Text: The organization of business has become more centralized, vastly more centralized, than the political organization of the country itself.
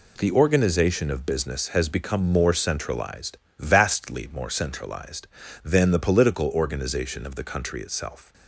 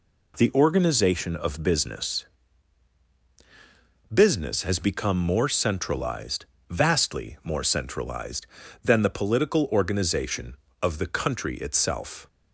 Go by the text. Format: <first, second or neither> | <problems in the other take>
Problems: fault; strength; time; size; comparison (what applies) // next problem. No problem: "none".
first | says "business" twice; at 4.1 s